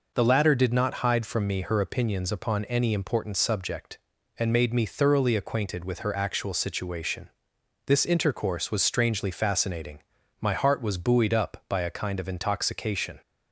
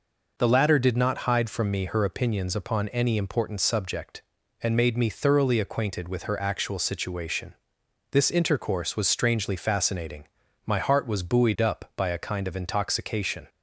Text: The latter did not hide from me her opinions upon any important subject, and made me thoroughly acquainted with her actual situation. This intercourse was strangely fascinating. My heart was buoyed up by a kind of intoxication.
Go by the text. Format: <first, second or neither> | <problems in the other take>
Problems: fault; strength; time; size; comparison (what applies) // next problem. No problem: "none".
neither | none